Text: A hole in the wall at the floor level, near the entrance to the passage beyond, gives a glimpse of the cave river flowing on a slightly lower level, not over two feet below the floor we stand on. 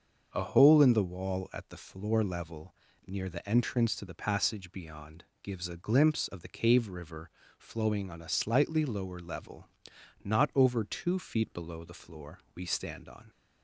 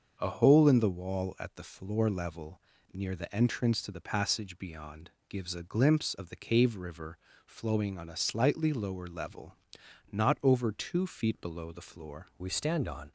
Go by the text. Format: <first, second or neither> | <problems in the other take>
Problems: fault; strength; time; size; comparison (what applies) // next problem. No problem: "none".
first | starts louder than the rest; until 1.2 s; 6.5 dB; also in the first // pauses between "river" and "flowing"; slight; at 7.1 s; 0.28 s long; slight in the first // changes voice at "we"; from 12.3 s on; 0.8 s long